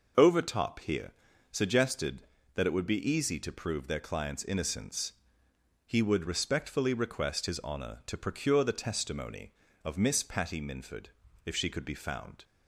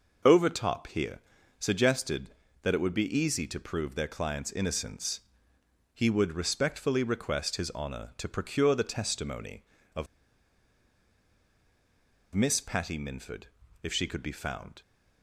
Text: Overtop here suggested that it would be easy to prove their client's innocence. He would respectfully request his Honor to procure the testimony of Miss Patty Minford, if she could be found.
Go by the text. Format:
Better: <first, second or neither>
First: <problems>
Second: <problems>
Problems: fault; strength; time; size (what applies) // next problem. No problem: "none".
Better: first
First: pauses between "here" and "suggested"; at 1.1 s; 0.40 s long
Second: pauses between "here" and "suggested"; at 1.1 s; 0.40 s long // pauses between "of" and "Miss"; strong; at 10.0 s; 2.2 s long